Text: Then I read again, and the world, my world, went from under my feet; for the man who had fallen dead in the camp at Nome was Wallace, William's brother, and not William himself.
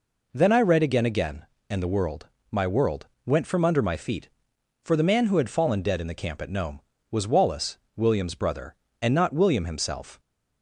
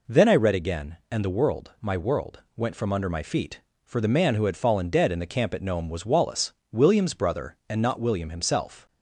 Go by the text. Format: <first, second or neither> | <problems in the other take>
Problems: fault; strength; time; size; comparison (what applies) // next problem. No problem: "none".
second | says "again" twice; at 1.0 s